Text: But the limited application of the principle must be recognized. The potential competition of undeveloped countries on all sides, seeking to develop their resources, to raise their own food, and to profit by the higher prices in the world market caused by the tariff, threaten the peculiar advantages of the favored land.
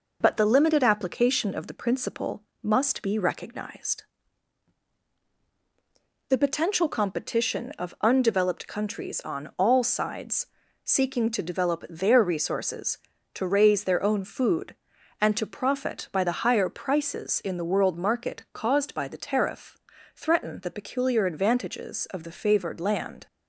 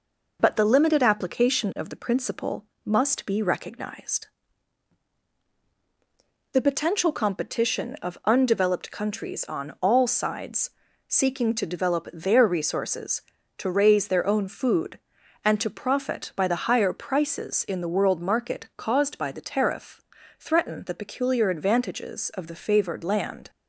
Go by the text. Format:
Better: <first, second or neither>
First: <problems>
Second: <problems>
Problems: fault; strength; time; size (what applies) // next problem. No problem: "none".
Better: neither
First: pauses between "principle" and "must"; slight; at 2.4 s; 0.18 s long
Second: pauses between "principle" and "must"; slight; at 2.6 s; 0.18 s long